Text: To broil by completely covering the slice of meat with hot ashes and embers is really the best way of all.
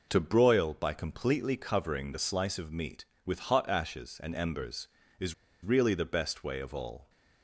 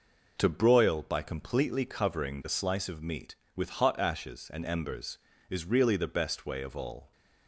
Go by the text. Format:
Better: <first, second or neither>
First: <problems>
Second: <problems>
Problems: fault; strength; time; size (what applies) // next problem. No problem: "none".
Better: second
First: pauses between "is" and "really"; slight; at 5.3 s; 0.29 s long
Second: none